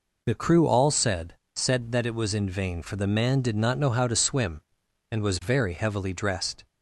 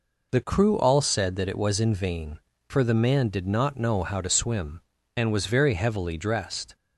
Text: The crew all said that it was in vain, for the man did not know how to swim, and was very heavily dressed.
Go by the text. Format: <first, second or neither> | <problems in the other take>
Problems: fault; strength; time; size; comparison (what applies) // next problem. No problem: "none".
second | says "said" twice; at 1.5 s